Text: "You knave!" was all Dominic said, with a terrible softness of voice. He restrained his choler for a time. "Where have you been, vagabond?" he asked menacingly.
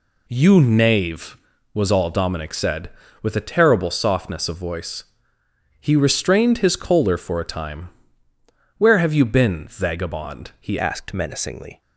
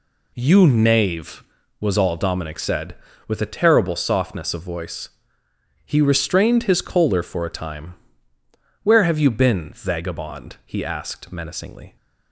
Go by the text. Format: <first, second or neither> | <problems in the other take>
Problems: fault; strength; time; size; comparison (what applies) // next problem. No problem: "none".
second | changes voice at "asked"; from 10.7 s on; 1.1 s long